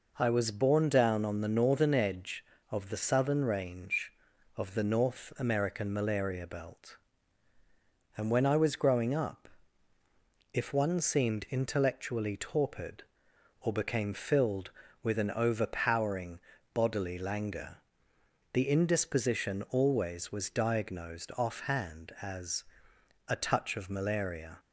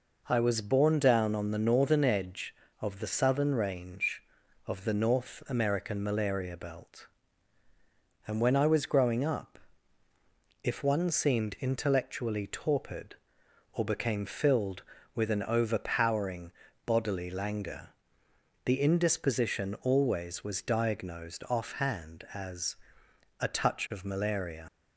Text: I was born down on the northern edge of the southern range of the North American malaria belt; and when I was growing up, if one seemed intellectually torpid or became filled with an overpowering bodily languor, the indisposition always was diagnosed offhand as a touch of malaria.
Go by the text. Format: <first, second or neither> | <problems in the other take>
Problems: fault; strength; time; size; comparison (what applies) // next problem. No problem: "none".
first | pauses between "overpowering" and "bodily"; slight; at 16.5 s; 0.34 s long; slight in the first // pauses between "as" and "a"; noticeable; at 22.7 s; 0.66 s long; noticeable in the first // leaves "malaria" unfinished; at 24.6 s; 65 ms